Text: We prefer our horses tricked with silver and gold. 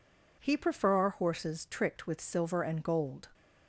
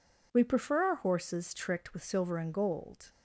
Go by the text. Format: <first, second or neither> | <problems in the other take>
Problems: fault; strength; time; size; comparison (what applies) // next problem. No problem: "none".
second | says "He" for "We"; at 0.3 s